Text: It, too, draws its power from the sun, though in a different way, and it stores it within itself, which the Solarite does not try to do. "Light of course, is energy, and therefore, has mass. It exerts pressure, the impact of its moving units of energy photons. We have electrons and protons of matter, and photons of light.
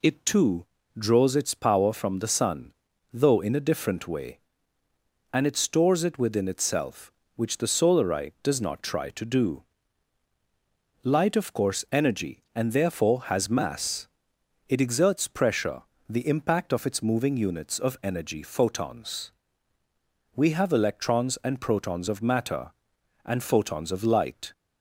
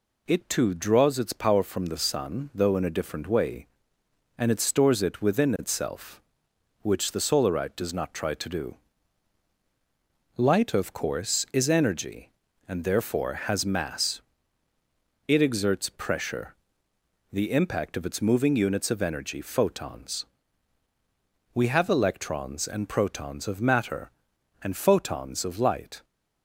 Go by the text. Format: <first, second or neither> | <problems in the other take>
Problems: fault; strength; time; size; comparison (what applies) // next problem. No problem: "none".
second | skips "is"; at 11.8 s